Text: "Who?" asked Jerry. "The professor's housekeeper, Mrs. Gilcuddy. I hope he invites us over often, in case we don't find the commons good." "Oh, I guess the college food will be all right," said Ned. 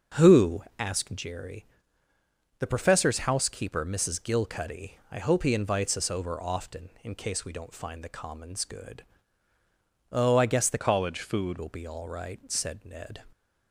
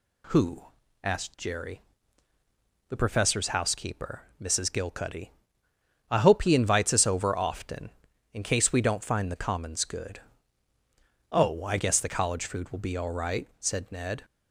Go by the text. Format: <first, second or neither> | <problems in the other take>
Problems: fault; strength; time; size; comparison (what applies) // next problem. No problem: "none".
second | starts louder than the rest; until 1.3 s; 6.5 dB // changes voice from "college" to "food"; from 10.7 to 11.5 s; 0.8 s long